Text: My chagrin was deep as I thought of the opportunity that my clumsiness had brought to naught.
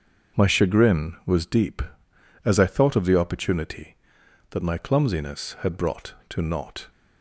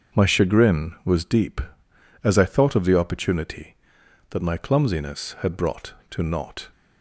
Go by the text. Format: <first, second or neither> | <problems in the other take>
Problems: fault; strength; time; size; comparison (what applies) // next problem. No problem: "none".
neither | starts louder than the rest; the same in both